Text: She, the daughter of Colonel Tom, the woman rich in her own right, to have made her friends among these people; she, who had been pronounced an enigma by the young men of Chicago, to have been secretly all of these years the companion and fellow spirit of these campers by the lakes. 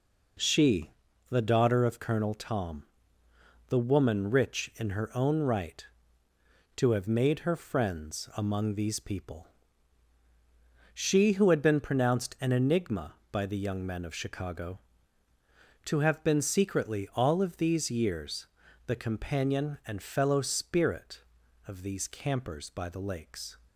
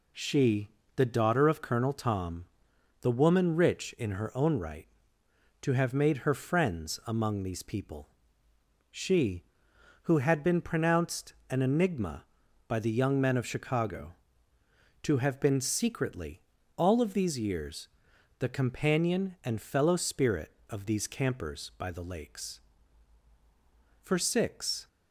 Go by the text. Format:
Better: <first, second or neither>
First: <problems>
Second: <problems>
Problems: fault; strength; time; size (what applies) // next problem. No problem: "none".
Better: first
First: pauses between "years" and "the"; at 18.4 s; 0.40 s long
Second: pauses between "pronounced" and "an"; slight; at 11.3 s; 0.16 s long // pauses between "secretly" and "all"; at 16.3 s; 0.38 s long // pauses between "years" and "the"; noticeable; at 17.8 s; 0.50 s long // goes on to say "For six"; noticeable; from 24.0 s on; 0.86 s long